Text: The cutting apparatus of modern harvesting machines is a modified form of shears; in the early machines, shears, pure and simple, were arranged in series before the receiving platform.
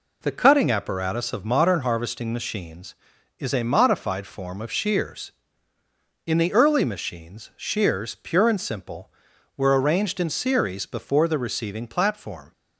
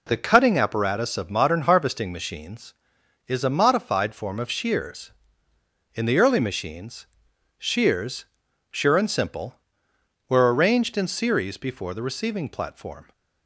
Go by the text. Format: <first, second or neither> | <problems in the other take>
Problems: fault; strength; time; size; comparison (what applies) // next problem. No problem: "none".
first | says "sure" for "pure"; at 8.7 s